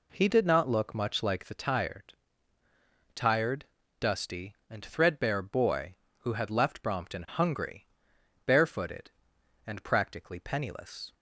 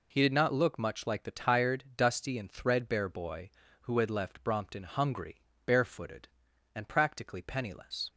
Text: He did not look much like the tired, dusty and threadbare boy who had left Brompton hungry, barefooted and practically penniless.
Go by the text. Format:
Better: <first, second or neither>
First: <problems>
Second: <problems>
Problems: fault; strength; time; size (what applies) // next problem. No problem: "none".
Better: second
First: says "tired" twice; at 3.1 s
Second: none